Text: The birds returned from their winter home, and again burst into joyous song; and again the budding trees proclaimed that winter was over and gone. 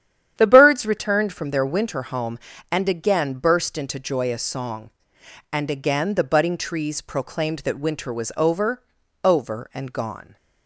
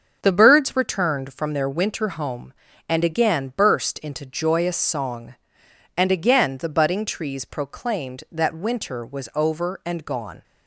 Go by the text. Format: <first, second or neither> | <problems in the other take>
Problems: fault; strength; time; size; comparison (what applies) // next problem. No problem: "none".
second | starts louder than the rest; strong; until 1.3 s; 10 dB; also in the second // says "over" twice; at 9.2 s